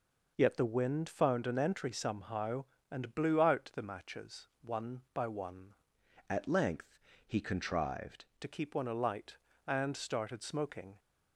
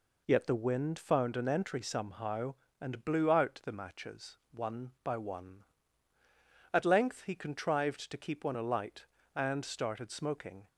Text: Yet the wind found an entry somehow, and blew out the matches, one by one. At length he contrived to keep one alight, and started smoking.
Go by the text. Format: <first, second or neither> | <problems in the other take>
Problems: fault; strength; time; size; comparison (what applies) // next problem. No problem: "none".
second | changes voice from "At" to "contrived"; from 6.2 to 8.2 s; 2.0 s long // pauses between "length" and "he"; slight; at 6.9 s; 0.26 s long